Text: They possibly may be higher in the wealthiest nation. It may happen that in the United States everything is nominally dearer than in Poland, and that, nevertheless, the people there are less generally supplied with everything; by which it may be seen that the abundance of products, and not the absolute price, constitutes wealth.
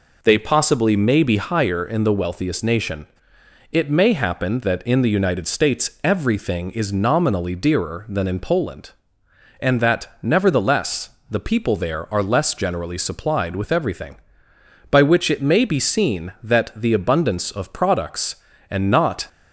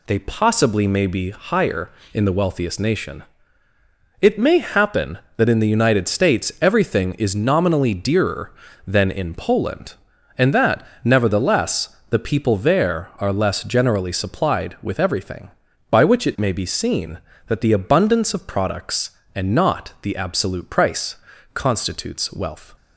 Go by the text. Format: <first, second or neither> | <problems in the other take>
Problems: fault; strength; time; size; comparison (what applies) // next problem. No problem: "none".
second | stops before "the absolute price constitutes wealth"; at 19.2 s